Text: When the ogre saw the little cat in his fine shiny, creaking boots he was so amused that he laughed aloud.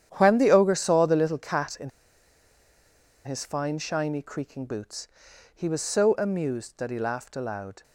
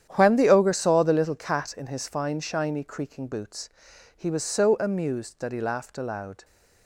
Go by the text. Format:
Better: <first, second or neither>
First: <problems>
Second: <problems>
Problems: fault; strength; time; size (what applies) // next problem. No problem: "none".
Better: second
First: starts louder than the rest; strong; until 1.1 s; 9.5 dB // pauses between "in" and "his"; strong; at 1.9 s; 1.3 s long // pauses between "boots" and "he"; noticeable; at 5.0 s; 0.46 s long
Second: starts louder than the rest; strong; until 1.1 s; 9.5 dB // pauses between "boots" and "he"; noticeable; at 3.6 s; 0.46 s long